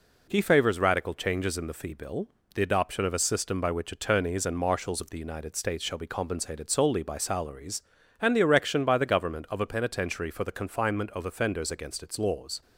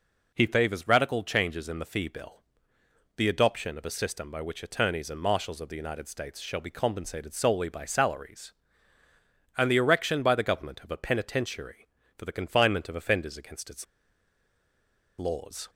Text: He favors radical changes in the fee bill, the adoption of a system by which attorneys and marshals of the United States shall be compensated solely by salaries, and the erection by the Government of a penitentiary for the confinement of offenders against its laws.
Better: first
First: none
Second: pauses between "its" and "laws"; strong; at 13.8 s; 1.3 s long

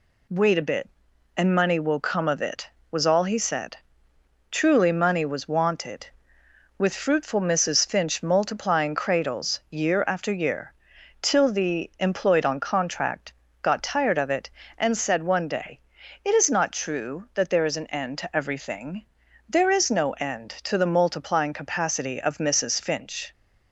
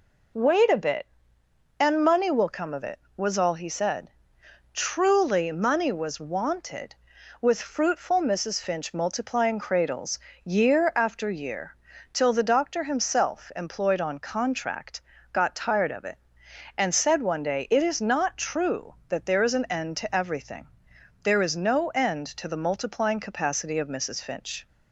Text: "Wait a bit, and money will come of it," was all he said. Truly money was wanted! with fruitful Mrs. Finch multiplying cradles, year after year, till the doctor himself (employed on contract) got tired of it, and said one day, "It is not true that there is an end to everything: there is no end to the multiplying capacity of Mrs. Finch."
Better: second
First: skips "doctor himself"; at 11.9 s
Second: none

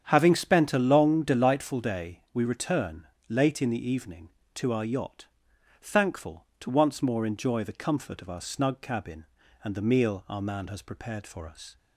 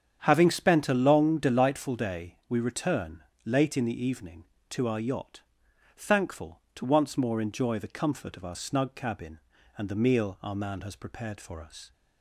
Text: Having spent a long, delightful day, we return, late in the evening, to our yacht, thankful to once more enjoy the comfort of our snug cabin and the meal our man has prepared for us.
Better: neither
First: starts louder than the rest; strong; until 1.1 s; 8.5 dB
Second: starts louder than the rest; strong; until 1.2 s; 8.5 dB

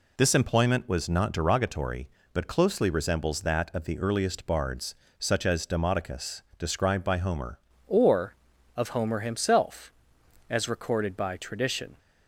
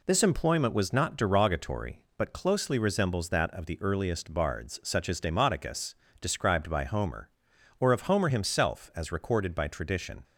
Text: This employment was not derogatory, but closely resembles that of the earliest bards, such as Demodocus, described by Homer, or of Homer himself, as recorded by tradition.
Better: second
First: changes voice at "or"; from 7.8 s on; 4.1 s long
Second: none

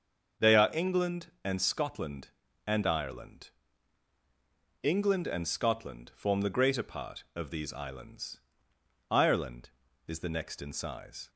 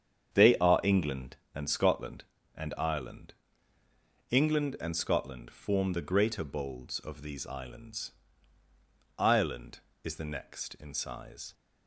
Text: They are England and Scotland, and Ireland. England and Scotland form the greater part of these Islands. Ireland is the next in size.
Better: first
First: starts louder than the rest; until 1.5 s; 6.5 dB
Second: starts louder than the rest; strong; until 1.6 s; 8 dB // says "bolds" for "part"; at 6.4 s

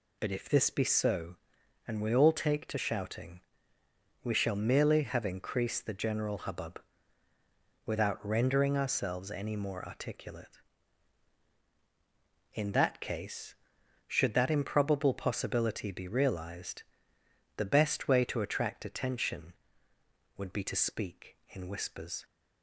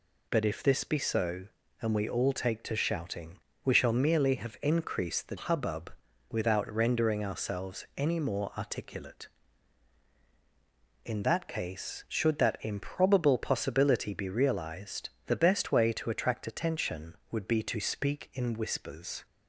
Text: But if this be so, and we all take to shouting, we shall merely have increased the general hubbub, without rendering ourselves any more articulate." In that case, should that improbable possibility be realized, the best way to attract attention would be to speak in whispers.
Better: first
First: none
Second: skips "general"; at 5.3 s

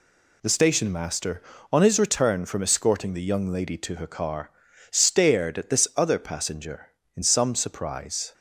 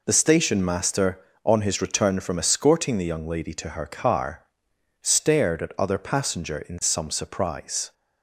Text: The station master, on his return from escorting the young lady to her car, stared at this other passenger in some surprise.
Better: first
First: none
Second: skips "this"; at 5.7 s

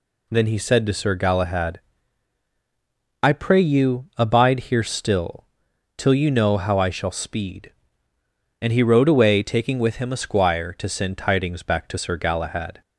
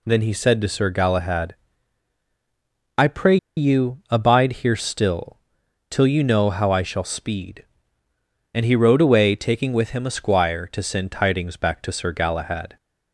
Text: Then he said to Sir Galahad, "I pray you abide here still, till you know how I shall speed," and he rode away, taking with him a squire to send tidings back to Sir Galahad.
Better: first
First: none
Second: pauses between "pray" and "you"; slight; at 3.3 s; 0.20 s long

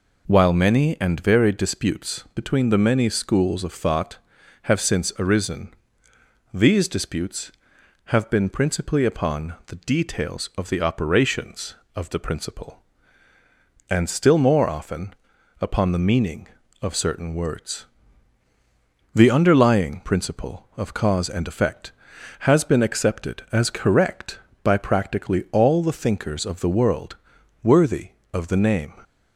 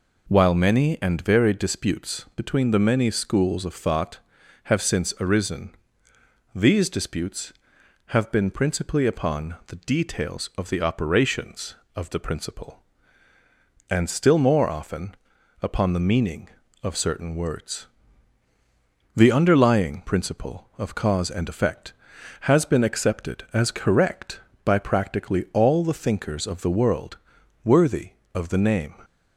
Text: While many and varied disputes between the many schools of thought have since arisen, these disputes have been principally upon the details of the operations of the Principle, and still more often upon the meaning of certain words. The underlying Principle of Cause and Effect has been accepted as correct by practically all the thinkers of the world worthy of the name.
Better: neither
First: pauses between "often" and "upon"; noticeable; at 15.1 s; 0.48 s long // pauses between "world" and "worthy"; noticeable; at 27.1 s; 0.46 s long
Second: pauses between "often" and "upon"; noticeable; at 15.1 s; 0.48 s long // pauses between "world" and "worthy"; noticeable; at 27.1 s; 0.46 s long

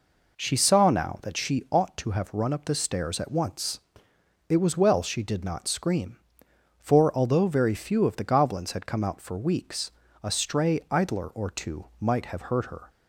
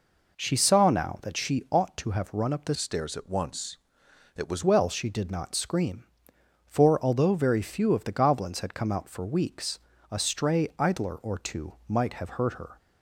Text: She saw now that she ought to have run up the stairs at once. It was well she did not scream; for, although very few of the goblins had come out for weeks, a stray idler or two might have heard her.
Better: first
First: none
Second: changes voice from "stairs" to "was"; from 2.7 to 4.6 s; 1.9 s long

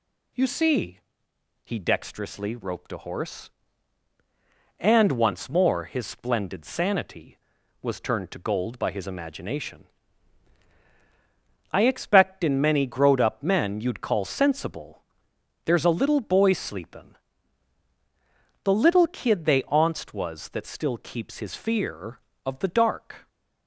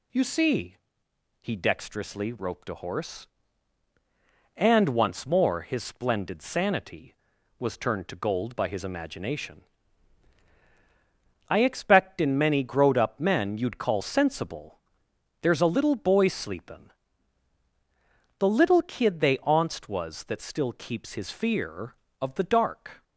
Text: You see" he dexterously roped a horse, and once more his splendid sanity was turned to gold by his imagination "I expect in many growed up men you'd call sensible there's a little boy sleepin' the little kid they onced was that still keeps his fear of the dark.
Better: neither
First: pauses between "see" and "he"; noticeable; at 0.9 s; 0.68 s long // pauses between "imagination" and "I"; strong; at 9.8 s; 1.8 s long // pauses between "sensible" and "there's"; noticeable; at 15.0 s; 0.64 s long // pauses between "sleepin" and "the"; strong; at 17.1 s; 1.4 s long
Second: pauses between "see" and "he"; noticeable; at 0.7 s; 0.68 s long // pauses between "imagination" and "I"; strong; at 9.6 s; 1.8 s long // pauses between "sensible" and "there's"; noticeable; at 14.7 s; 0.64 s long // pauses between "sleepin" and "the"; strong; at 16.9 s; 1.4 s long

